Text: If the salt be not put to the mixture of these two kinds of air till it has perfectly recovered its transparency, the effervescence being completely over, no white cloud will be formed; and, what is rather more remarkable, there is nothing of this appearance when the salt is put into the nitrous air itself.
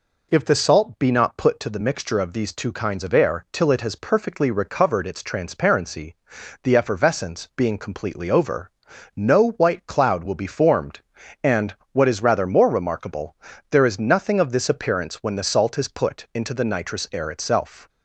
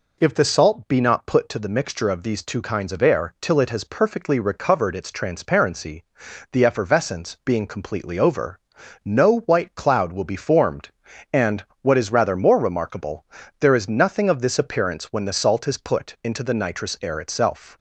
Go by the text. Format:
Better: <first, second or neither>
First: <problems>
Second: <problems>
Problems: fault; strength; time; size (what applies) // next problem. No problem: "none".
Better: neither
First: none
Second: none